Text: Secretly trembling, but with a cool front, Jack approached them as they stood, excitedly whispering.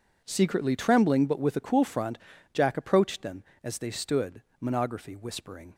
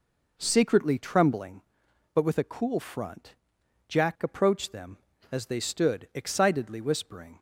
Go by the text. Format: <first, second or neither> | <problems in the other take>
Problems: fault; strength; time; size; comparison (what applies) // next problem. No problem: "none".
second | says "monography" for "excitedly"; at 4.6 s